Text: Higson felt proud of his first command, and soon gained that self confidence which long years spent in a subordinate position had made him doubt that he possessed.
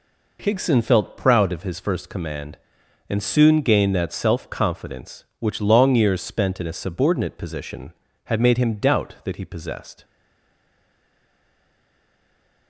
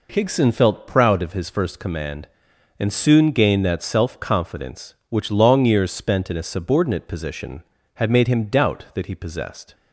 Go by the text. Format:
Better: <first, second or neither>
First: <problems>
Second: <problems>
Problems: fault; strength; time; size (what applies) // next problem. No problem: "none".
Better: second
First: stays silent after the last word; strong; from 10.0 s on; 2.6 s long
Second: none